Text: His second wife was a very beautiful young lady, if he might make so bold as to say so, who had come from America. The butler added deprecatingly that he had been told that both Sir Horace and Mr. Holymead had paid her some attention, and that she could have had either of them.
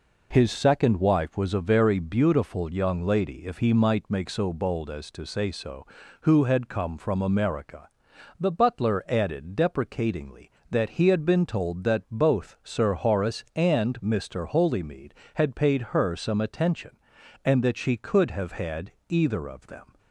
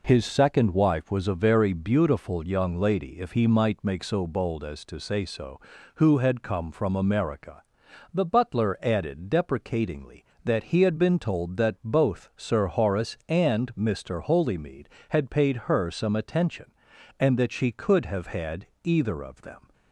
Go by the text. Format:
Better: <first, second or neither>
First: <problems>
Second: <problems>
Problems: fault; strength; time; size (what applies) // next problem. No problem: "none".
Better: neither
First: pauses between "had" and "either"; slight; at 18.9 s; 0.16 s long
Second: pauses between "had" and "either"; slight; at 18.6 s; 0.16 s long